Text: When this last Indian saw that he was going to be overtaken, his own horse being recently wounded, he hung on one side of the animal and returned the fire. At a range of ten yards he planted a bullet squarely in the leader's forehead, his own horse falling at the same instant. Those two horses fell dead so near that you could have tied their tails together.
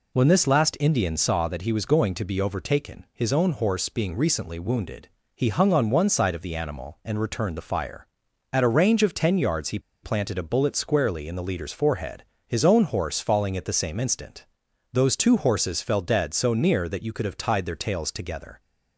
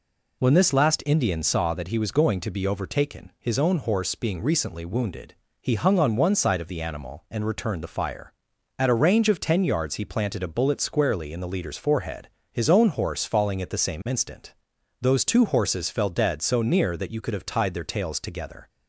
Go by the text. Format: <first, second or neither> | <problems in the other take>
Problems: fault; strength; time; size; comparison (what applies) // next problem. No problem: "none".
second | pauses between "he" and "planted"; slight; at 9.7 s; 0.24 s long